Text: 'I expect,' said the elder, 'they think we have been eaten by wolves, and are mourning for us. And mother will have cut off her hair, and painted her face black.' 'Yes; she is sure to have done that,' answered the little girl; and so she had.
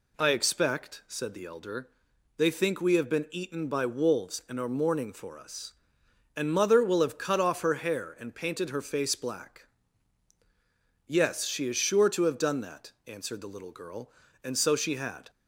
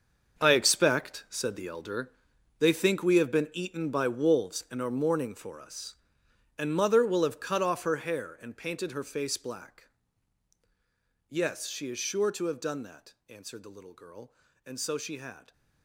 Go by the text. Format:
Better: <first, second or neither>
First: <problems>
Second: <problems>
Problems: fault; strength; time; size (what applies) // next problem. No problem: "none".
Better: first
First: none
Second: gets quieter; strong; throughout; 12.5 dB